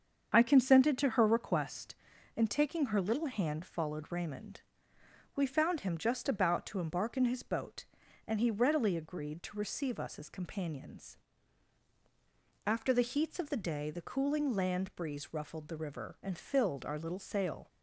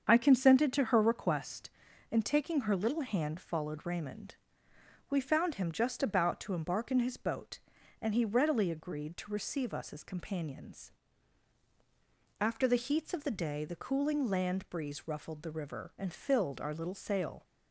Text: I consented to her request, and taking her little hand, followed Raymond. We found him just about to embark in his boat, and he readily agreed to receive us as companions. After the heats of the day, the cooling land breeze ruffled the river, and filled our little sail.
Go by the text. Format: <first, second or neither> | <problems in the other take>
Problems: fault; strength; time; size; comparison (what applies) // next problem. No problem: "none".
neither | starts louder than the rest; the same in both